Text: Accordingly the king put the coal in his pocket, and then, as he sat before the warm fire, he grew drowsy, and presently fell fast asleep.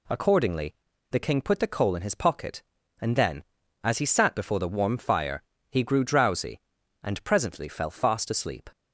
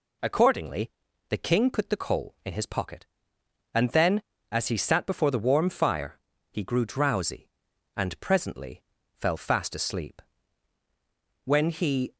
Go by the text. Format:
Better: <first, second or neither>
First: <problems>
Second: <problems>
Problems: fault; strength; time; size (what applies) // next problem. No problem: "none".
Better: first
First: pauses between "Accordingly" and "the"; at 0.7 s; 0.36 s long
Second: pauses between "Accordingly" and "the"; at 0.8 s; 0.40 s long // pauses between "presently" and "fell"; slight; at 8.8 s; 0.36 s long // goes on to say "When he"; noticeable; from 11.4 s on; 0.70 s long